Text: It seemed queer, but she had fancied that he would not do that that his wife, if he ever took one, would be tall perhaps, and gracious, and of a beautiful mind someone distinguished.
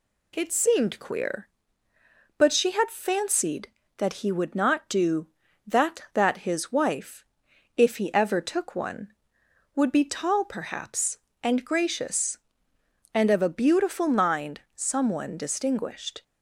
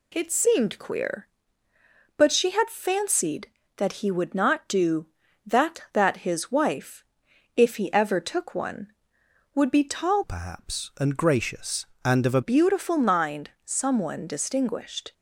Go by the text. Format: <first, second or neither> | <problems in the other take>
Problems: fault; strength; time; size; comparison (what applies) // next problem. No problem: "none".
first | changes voice from "perhaps" to "a"; from 10.2 to 12.4 s; 2.2 s long